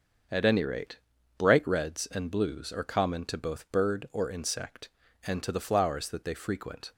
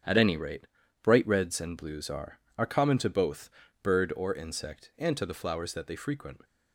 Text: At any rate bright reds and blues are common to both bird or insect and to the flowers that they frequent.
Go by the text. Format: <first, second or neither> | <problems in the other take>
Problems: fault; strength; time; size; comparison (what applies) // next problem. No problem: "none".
first | starts louder than the rest; strong; until 1.4 s; 8.5 dB; also in the first // pauses between "rate" and "bright"; slight; at 0.6 s; 0.36 s long; also in the first // says "are" twice; at 2.5 s // pauses between "both" and "bird"; slight; at 3.4 s; 0.32 s long